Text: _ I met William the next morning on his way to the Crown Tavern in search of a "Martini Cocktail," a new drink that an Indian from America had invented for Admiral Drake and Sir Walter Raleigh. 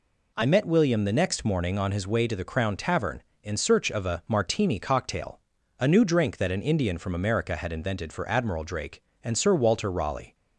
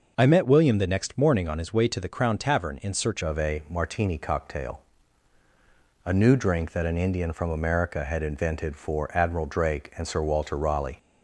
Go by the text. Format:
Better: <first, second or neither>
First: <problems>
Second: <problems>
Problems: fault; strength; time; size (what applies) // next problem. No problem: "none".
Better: first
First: none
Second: changes voice at "of"; from 3.2 s on; 7.7 s long